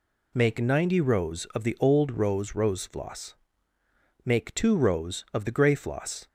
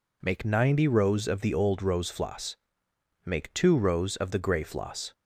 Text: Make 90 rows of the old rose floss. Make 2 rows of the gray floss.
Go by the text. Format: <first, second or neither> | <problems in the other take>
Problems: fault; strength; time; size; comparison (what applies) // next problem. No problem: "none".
second | says "rose" twice; at 2.5 s